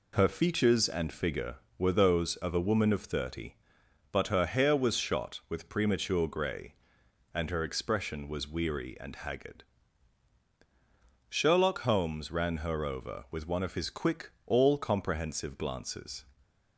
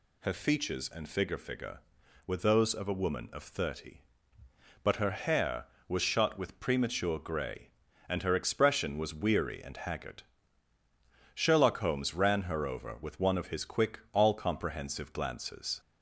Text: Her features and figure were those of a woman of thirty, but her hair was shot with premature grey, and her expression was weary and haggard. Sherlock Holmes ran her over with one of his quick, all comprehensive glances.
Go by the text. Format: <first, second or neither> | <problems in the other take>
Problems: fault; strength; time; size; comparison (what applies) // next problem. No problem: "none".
first | says "figure" twice; at 1.3 s